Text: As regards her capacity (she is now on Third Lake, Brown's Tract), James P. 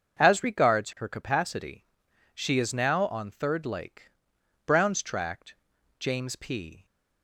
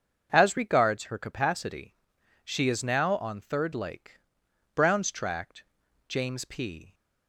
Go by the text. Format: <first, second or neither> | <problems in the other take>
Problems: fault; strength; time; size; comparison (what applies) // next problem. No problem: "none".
neither | starts louder than the rest; the same in both